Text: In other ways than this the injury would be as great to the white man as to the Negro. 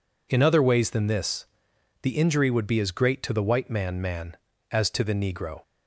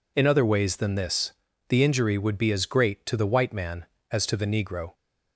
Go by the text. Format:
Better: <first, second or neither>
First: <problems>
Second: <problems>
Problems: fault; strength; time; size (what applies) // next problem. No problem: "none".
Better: second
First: pauses between "this" and "the"; noticeable; at 1.4 s; 0.56 s long // says "man" twice; at 3.9 s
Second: pauses between "this" and "the"; at 1.3 s; 0.38 s long